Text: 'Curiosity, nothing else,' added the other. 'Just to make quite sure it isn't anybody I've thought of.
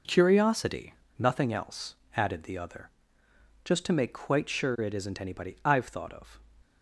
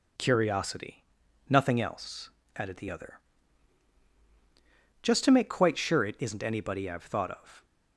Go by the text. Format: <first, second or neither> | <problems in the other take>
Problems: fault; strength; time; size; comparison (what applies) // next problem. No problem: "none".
neither | none